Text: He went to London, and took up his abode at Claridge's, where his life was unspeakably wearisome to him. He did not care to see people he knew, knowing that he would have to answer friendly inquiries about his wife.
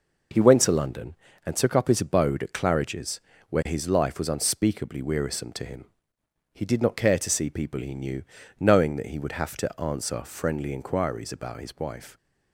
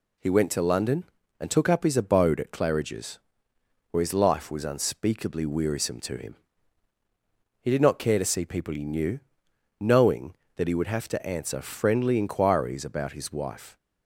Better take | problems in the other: neither | none

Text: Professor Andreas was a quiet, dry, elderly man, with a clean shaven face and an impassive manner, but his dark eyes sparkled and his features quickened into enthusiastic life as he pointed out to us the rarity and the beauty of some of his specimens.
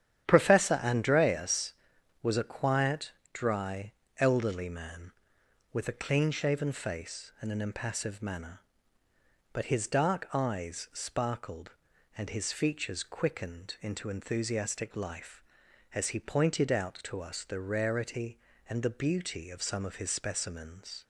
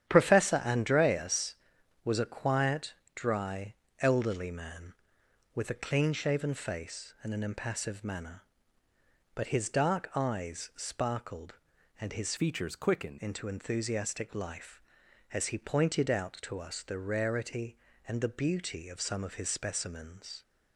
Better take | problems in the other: first | starts louder than the rest; strong; until 1.1 s; 10 dB; strong in the first // changes voice from "features" to "quickened"; from 12.3 to 13.1 s; 0.8 s long

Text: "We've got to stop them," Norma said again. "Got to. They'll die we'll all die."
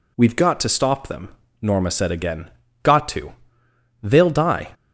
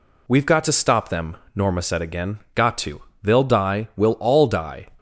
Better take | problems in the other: second | stops before "we'll all die"; at 4.7 s

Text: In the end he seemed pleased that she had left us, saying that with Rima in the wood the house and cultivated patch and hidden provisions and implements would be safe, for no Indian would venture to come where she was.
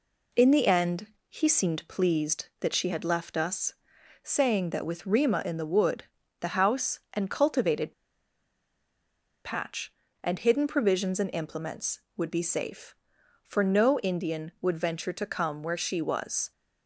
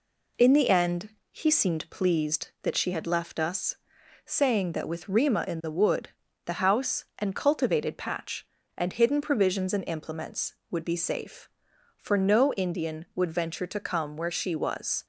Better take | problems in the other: second | pauses between "end" and "he"; slight; at 1.0 s; 0.20 s long; slight in the second // pauses between "wood" and "the"; slight; at 6.0 s; 0.36 s long; slight in the second // pauses between "cultivated" and "patch"; strong; at 7.9 s; 1.5 s long

